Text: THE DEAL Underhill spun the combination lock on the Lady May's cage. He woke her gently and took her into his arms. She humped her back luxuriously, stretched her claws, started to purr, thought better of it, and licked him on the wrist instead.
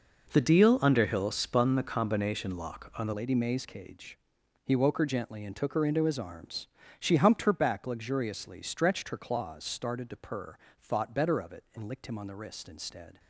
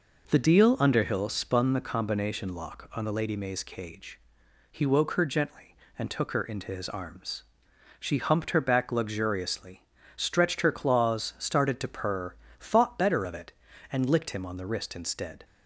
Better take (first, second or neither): second